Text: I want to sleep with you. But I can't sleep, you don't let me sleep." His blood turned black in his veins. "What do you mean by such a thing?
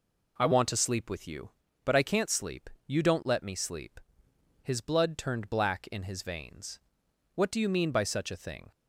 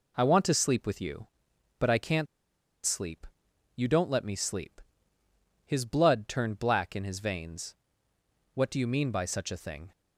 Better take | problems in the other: first | pauses between "can't" and "sleep"; noticeable; at 2.2 s; 0.59 s long

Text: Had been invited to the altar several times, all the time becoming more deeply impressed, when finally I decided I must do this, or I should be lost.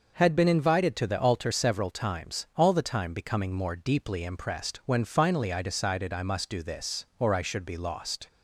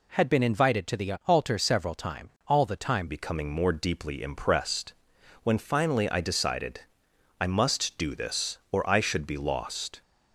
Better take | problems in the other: first | changes voice at "becoming"; from 3.0 s on; 7.0 s long // pauses between "decided" and "I"; noticeable; at 6.8 s; 0.58 s long

